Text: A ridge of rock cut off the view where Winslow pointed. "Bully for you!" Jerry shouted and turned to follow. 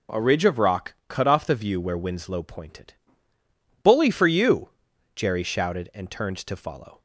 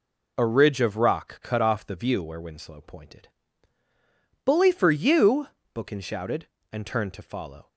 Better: first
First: none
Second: says "Bookin" for "Jerry"; at 5.7 s

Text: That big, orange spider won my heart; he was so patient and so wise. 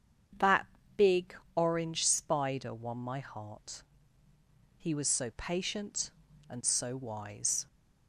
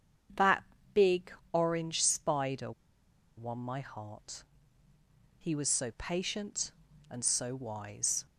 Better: first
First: starts louder than the rest; strong; until 1.9 s; 7 dB // pauses between "That" and "big"; slight; at 0.6 s; 0.30 s long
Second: starts louder than the rest; strong; until 1.8 s; 7 dB // pauses between "That" and "big"; slight; at 0.6 s; 0.30 s long // pauses between "spider" and "won"; noticeable; at 2.7 s; 0.66 s long

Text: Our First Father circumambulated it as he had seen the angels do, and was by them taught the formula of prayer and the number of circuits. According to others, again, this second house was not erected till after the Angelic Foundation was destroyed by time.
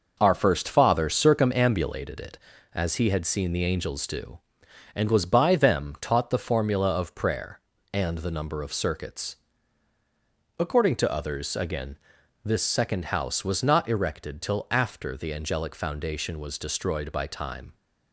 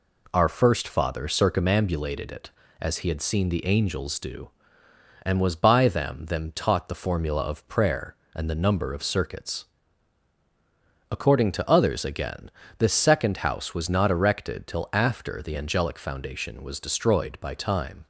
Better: first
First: none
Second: says "them" twice; at 6.2 s

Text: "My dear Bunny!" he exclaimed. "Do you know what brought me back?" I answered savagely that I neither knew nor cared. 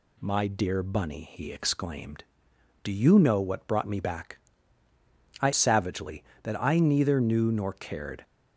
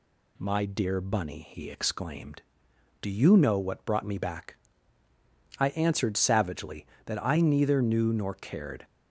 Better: second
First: skips "answered"; at 5.5 s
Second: none

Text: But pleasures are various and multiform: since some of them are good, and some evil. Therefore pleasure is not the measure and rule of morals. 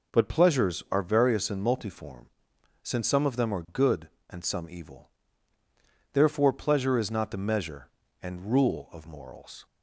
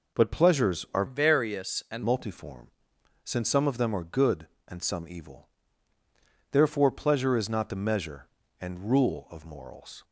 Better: first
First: none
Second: changes voice from "various" to "and"; from 1.0 to 2.0 s; 1.0 s long

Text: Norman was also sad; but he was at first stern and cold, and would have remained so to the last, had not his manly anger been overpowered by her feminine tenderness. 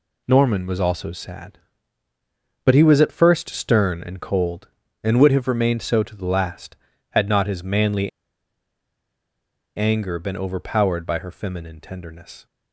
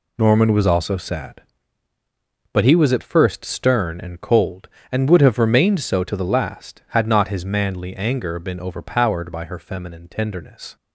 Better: second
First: pauses between "manly" and "anger"; strong; at 8.0 s; 1.6 s long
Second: none

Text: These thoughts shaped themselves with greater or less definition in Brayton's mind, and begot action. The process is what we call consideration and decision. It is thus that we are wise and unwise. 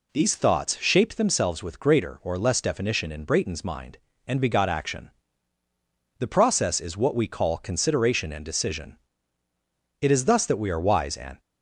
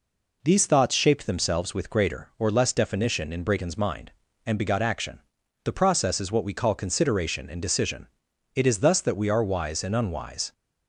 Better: second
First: stops before "unwise"; at 11.3 s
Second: none

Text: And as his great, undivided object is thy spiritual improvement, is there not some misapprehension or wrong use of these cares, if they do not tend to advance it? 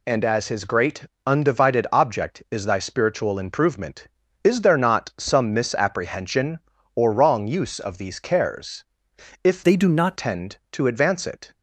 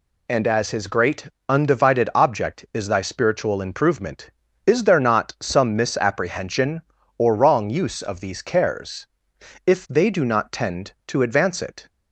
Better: second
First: changes voice from "they" to "not"; from 9.6 to 10.1 s; 0.5 s long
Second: none

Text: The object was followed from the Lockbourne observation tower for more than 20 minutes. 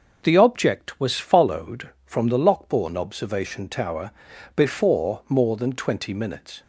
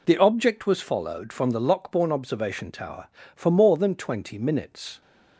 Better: second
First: starts louder than the rest; noticeable; until 1.2 s; 6 dB // says "before" for "for"; at 4.5 s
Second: none

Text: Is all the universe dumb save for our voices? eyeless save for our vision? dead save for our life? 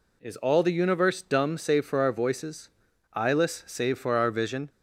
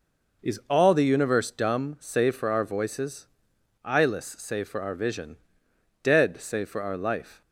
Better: second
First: stops before "dead save for our life"; at 4.6 s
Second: none

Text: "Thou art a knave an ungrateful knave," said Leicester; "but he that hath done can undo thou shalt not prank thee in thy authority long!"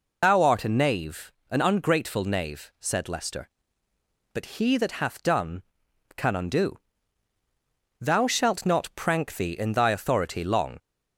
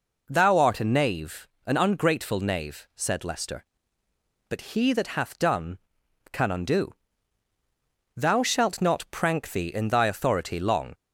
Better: second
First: loses the start of "Thou"; at 0.2 s; 105 ms // pauses between "knave" and "an"; slight; at 1.3 s; 0.18 s long // pauses between "undo" and "thou"; at 6.7 s; 1.2 s long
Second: pauses between "knave" and "an"; slight; at 1.4 s; 0.18 s long // pauses between "undo" and "thou"; at 6.9 s; 1.2 s long

